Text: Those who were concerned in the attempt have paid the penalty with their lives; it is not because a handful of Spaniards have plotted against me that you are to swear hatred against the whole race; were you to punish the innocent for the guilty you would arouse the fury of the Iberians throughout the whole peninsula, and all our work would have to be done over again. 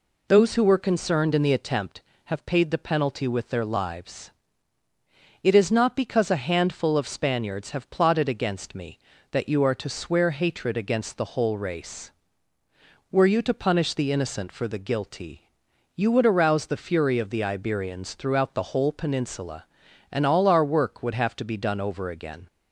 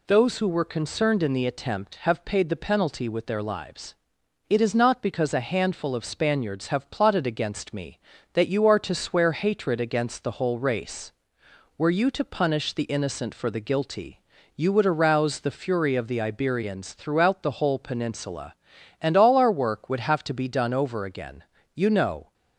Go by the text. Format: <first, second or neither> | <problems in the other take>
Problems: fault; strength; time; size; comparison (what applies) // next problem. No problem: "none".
first | pauses between "guilty" and "you"; at 14.1 s; 0.38 s long; noticeable in the first // goes on to say "You know"; from 21.7 s on; 0.58 s long